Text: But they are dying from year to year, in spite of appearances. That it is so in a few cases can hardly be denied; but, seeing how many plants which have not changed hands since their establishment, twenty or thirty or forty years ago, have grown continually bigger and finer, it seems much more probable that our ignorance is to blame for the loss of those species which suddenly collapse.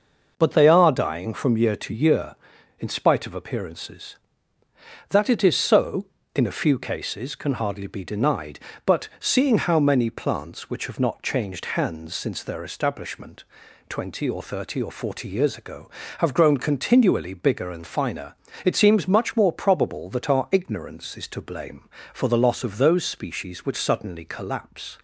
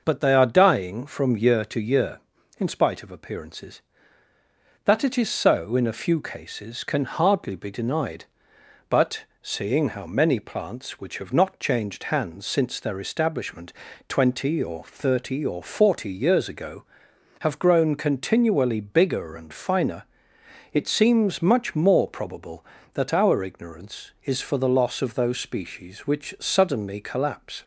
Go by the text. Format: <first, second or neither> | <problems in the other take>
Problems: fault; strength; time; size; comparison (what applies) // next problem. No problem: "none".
first | skips "to blame"; at 24.4 s